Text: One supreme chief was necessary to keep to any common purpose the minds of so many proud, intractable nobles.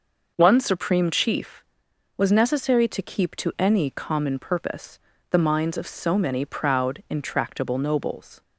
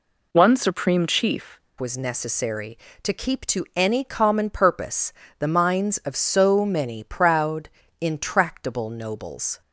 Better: first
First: pauses between "purpose" and "the"; slight; at 4.9 s; 0.32 s long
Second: changes voice at "was"; from 1.7 s on; 7.9 s long // pauses between "purpose" and "the"; slight; at 5.1 s; 0.24 s long

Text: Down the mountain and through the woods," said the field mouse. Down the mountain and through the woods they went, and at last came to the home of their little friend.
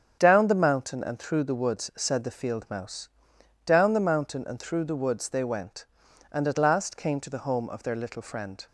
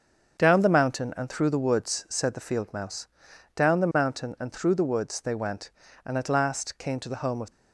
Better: first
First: starts louder than the rest; strong; until 1.2 s; 7.5 dB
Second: starts louder than the rest; until 1.4 s; 7 dB // stops before "their little friend"; at 7.5 s

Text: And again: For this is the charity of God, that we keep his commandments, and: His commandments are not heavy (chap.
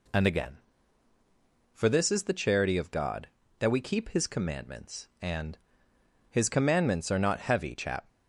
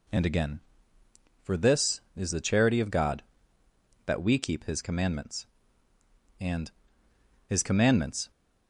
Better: first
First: none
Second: stops before "are not heavy chap"; at 8.3 s

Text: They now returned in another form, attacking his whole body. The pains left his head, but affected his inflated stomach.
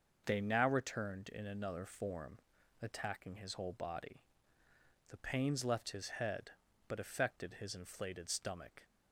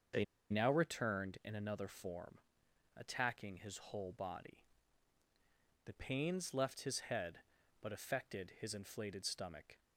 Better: first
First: none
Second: starts louder than the rest; until 1.4 s; 6.5 dB // pauses between "They" and "now"; slight; at 0.2 s; 0.26 s long

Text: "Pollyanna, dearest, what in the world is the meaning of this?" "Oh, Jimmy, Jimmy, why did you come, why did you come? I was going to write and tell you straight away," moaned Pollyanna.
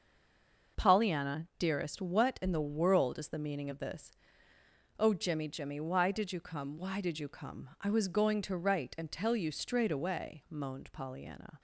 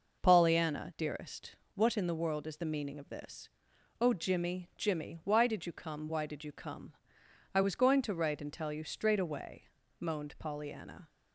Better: second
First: stays silent before the first word; slight; until 0.7 s; 0.7 s long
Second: none

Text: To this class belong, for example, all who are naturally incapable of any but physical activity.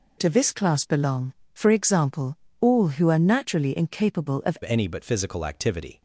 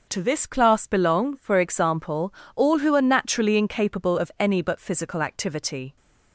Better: second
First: changes voice at "any"; from 4.6 s on; 1.4 s long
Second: none

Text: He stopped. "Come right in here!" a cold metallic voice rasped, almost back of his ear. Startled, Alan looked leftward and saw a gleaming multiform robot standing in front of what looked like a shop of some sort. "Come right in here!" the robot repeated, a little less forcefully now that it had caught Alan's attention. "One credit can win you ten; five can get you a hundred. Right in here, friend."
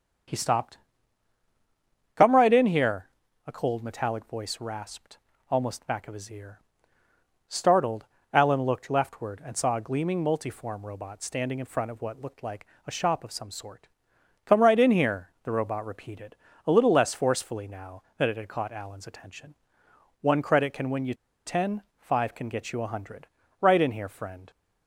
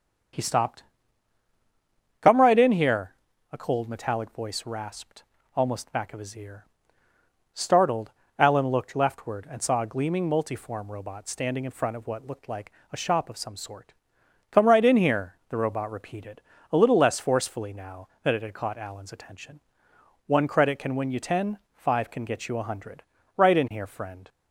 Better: second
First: starts louder than the rest; strong; until 2.6 s; 7 dB // pauses between "like" and "a"; slight; at 12.6 s; 0.18 s long // pauses between "you" and "ten"; slight; at 21.1 s; 0.31 s long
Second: starts louder than the rest; strong; until 2.7 s; 7 dB // pauses between "like" and "a"; slight; at 12.7 s; 0.18 s long

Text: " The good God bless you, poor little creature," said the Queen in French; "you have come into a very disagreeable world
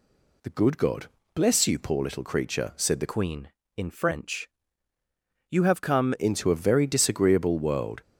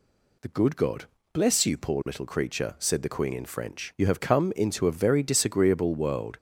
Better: second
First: pauses between "God" and "bless"; slight; at 1.0 s; 0.28 s long // changes voice from "Queen" to "come"; from 3.1 to 6.1 s; 3.0 s long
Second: pauses between "God" and "bless"; slight; at 1.0 s; 0.28 s long

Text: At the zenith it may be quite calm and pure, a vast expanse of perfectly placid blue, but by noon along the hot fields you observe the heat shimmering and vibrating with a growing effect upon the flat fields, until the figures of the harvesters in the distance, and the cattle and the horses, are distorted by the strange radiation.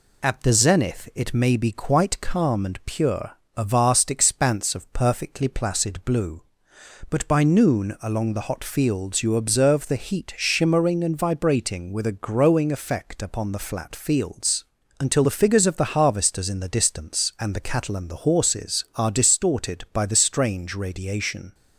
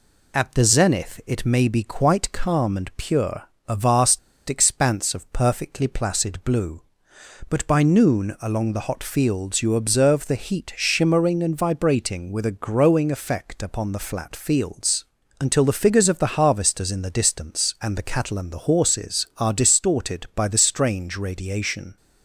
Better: first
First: none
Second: pauses between "vast" and "expanse"; slight; at 4.1 s; 0.28 s long

